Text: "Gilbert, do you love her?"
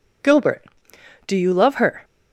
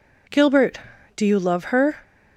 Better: neither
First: none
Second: none

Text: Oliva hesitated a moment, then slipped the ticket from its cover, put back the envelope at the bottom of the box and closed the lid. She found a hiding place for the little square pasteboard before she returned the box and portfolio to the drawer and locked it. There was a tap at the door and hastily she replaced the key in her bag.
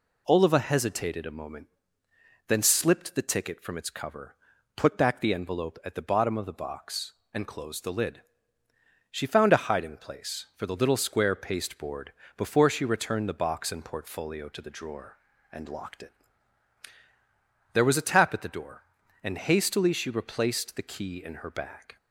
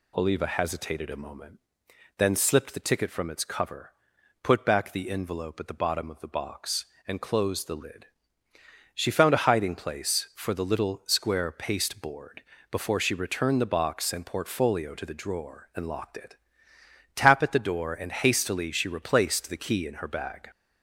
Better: first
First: pauses between "pasteboard" and "before"; slight; at 12.1 s; 0.26 s long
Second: pauses between "pasteboard" and "before"; slight; at 12.4 s; 0.28 s long // skips "There was a"; at 16.7 s

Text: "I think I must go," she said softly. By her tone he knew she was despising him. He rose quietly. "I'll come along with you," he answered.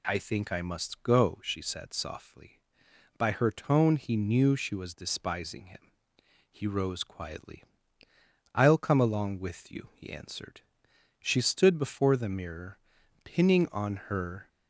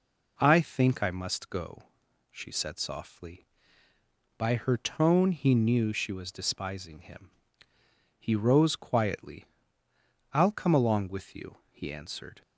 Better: second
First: goes on to say "She stood before the mirror pinning on her"; strong; from 11.1 s on; 3.2 s long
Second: none

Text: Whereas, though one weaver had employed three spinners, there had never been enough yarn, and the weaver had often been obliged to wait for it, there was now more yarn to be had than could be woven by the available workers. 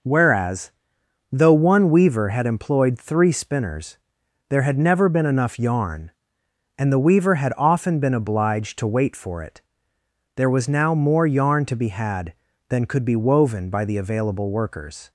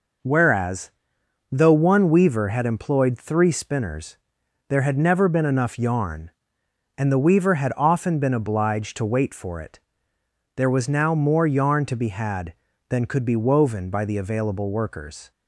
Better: neither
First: none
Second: none

